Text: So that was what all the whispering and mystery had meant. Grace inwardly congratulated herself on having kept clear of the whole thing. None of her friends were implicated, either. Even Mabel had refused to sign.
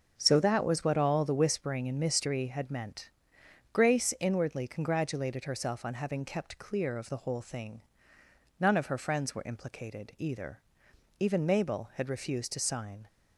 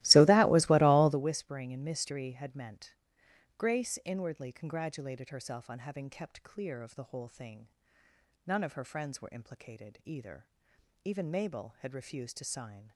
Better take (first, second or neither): first